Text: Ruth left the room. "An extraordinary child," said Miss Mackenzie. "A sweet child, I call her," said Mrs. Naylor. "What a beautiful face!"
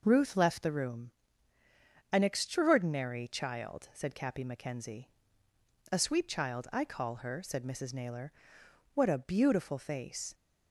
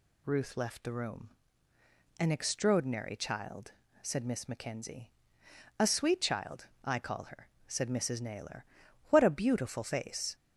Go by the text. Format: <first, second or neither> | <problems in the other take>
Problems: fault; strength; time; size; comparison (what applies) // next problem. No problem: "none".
second | says "Cappy" for "Miss"; at 4.1 s